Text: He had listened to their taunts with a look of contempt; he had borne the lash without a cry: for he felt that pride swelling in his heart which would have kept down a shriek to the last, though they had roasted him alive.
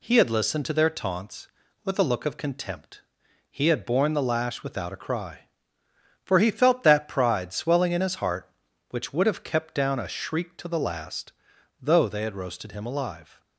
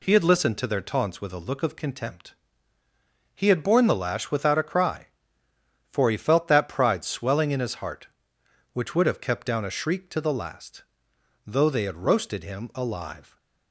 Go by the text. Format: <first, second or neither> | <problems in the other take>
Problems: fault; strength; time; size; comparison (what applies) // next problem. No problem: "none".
neither | none